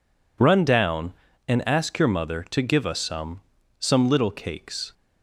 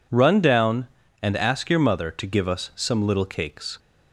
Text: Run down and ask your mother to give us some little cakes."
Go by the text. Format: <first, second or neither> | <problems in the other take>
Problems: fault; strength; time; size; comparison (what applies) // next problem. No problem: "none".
second | says "some" twice; at 3.8 s